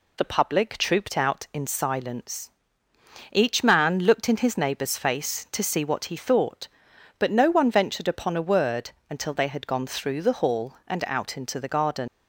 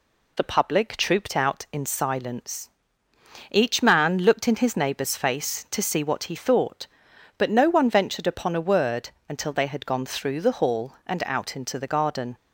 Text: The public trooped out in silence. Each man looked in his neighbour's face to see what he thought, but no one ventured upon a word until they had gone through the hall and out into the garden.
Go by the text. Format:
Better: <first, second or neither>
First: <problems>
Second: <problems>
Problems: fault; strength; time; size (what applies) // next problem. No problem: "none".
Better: second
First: pauses between "word" and "until"; slight; at 8.9 s; 0.18 s long // leaves "garden" unfinished; at 12.0 s; 85 ms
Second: pauses between "word" and "until"; slight; at 9.0 s; 0.18 s long